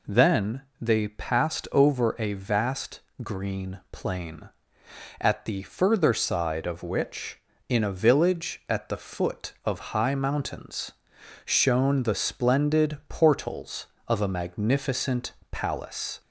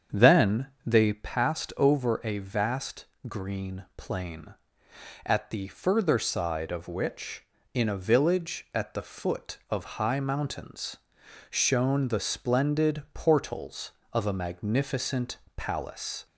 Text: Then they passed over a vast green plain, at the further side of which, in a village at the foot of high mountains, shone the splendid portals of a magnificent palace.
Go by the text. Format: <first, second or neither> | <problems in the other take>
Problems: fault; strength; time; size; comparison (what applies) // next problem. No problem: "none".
first | starts louder than the rest; strong; until 1.3 s; 7.5 dB // pauses between "Then" and "they"; slight; at 0.6 s; 0.20 s long; slight in the first // pauses between "vast" and "green"; slight; at 3.0 s; 0.22 s long; slight in the first // pauses between "magnificent" and "palace"; slight; at 15.3 s; 0.18 s long; slight in the first